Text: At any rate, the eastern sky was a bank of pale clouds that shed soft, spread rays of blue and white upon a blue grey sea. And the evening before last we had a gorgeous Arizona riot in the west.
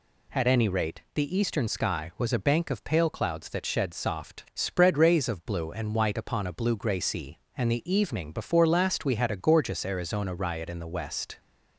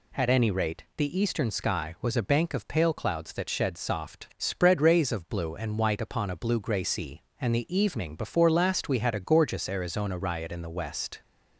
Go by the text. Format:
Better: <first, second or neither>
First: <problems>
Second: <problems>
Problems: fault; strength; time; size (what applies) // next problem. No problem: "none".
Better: neither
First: none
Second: none